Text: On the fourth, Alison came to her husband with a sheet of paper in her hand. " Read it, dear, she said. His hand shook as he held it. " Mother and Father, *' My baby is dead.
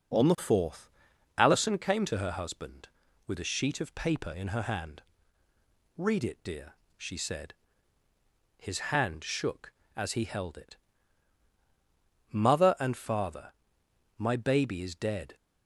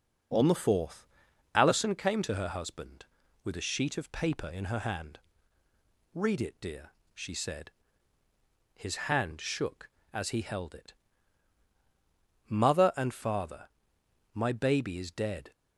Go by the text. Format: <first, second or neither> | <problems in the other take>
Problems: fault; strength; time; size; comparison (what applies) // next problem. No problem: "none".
neither | starts louder than the rest; strong; the same in both // pauses between "His" and "hand"; slight; the same in both